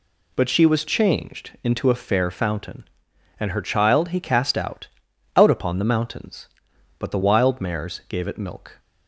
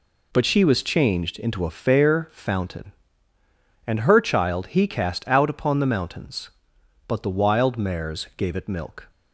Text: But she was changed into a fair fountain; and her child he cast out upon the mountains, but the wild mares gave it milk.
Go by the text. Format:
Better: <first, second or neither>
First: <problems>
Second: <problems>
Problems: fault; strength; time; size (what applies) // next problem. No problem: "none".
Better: second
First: says "out" twice; at 5.3 s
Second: none